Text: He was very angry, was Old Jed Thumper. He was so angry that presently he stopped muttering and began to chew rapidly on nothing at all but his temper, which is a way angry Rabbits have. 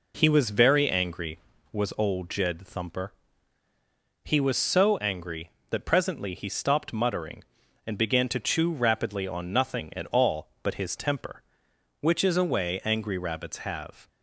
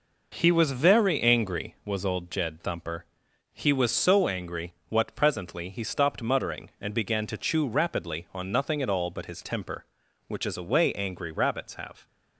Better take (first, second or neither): first